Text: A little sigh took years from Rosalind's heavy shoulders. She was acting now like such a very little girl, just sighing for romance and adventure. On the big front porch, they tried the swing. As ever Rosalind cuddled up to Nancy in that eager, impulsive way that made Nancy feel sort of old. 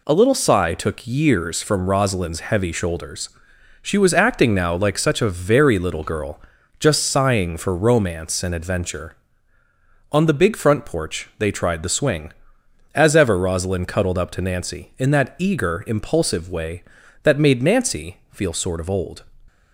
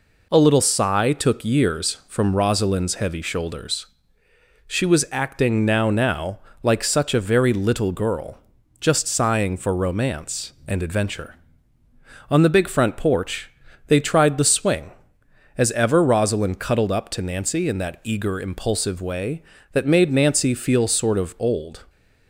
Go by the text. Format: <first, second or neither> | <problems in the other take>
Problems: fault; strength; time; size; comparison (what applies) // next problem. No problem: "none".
first | says "now" twice; at 5.9 s